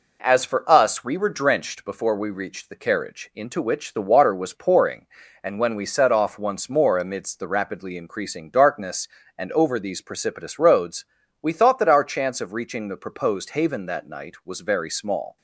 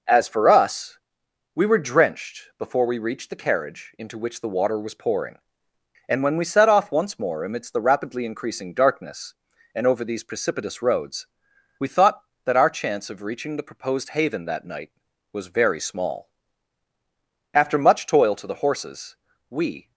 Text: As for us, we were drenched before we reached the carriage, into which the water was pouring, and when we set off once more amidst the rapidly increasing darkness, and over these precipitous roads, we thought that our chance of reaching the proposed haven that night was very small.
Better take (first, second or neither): first